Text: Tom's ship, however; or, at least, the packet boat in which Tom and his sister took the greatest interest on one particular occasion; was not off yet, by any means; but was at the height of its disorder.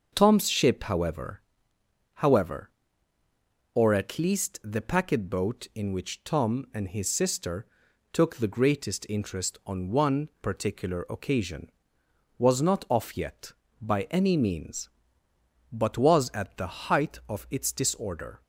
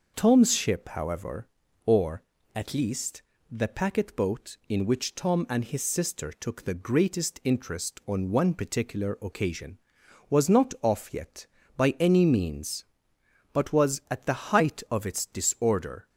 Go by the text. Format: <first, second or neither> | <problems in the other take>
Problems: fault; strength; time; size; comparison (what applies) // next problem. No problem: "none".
second | starts louder than the rest; until 1.1 s; 6.5 dB // says "however" twice; at 2.1 s // pauses between "sister" and "took"; noticeable; at 7.6 s; 0.48 s long